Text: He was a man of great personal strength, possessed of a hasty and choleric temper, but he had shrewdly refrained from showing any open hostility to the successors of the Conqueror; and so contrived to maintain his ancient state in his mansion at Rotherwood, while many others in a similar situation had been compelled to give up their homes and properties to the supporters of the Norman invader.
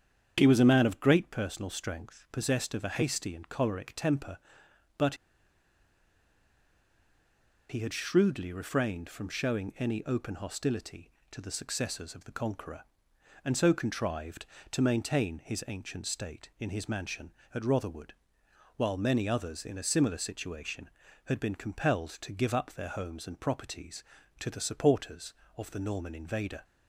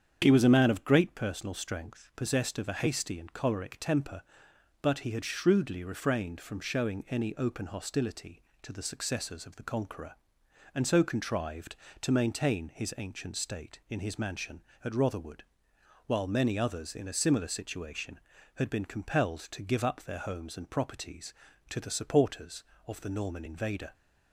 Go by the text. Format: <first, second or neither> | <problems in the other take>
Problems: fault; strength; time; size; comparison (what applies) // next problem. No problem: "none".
second | starts louder than the rest; strong; until 1.3 s; 8 dB; strong in the second // pauses between "but" and "he"; strong; at 5.1 s; 2.5 s long